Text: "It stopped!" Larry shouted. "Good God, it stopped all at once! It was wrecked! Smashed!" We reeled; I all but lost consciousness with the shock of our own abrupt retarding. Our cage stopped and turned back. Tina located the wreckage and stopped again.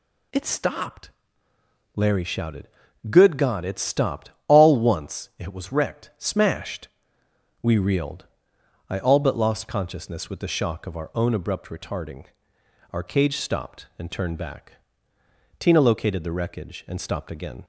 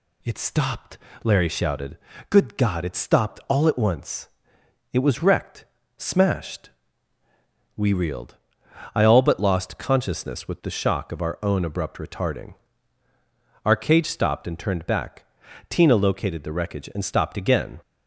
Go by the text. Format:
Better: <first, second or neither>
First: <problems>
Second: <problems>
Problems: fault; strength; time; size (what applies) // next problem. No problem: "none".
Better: second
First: pauses between "stopped" and "all"; slight; at 4.3 s; 0.18 s long // skips "at"; at 4.7 s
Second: none